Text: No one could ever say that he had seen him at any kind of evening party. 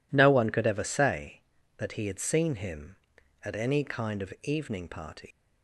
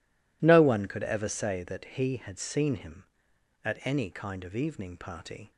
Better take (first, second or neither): second